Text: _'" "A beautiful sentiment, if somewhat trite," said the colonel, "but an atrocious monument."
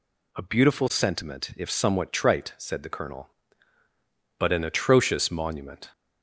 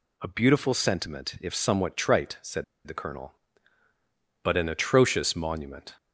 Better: first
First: none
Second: pauses between "said" and "the"; slight; at 2.6 s; 0.22 s long

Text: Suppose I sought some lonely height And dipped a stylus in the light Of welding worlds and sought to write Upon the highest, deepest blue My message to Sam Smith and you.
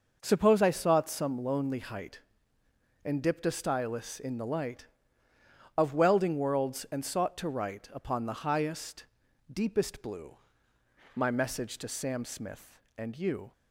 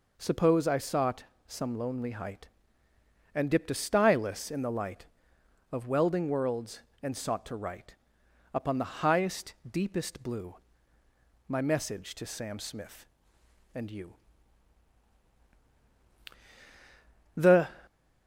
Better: first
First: pauses between "blue" and "My"; noticeable; at 10.3 s; 0.80 s long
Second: pauses between "sought" and "some"; slight; at 1.2 s; 0.24 s long // pauses between "write" and "Upon"; noticeable; at 7.9 s; 0.58 s long // pauses between "blue" and "My"; noticeable; at 10.5 s; 0.92 s long // goes on to say "The"; slight; from 17.3 s on; 0.32 s long

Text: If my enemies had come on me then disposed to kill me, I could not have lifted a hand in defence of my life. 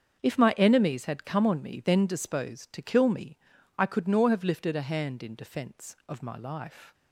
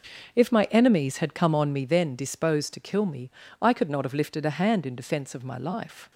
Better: second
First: starts louder than the rest; until 1.2 s; 7 dB // says "nor" for "not"; at 4.0 s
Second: starts louder than the rest; until 1.4 s; 6.5 dB

